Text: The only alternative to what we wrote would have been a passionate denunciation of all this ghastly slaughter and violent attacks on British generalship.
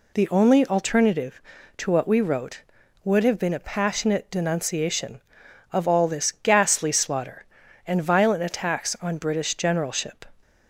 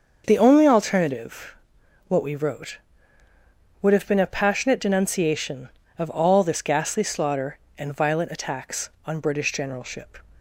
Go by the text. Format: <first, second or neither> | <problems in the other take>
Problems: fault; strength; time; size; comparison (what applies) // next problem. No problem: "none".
first | starts louder than the rest; until 1.2 s; 6.5 dB // skips "to"; at 1.8 s